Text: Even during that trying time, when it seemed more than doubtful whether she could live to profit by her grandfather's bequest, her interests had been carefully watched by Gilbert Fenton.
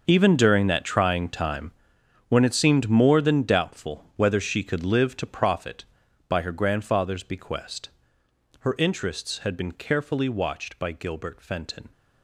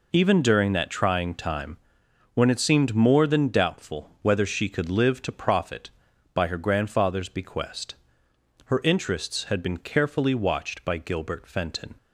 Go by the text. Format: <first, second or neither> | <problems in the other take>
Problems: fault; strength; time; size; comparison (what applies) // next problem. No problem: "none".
second | gets quieter; strong; throughout; 14 dB